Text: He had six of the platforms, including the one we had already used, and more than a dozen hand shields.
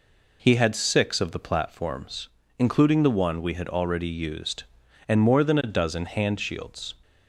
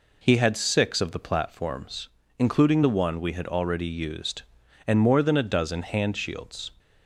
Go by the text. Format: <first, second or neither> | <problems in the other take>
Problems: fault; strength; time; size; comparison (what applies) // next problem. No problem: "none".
neither | none